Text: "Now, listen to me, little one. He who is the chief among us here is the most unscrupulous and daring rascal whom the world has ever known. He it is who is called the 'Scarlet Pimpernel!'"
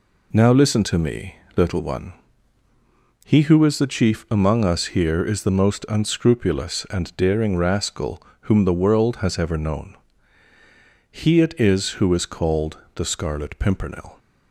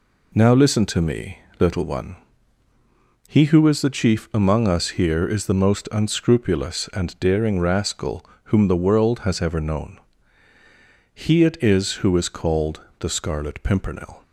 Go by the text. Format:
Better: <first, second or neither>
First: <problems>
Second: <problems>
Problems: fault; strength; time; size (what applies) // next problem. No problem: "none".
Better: neither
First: pauses between "rascal" and "whom"; slight; at 8.2 s; 0.20 s long // pauses between "called" and "the"; slight; at 12.7 s; 0.16 s long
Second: pauses between "rascal" and "whom"; slight; at 8.2 s; 0.20 s long // pauses between "called" and "the"; slight; at 12.8 s; 0.17 s long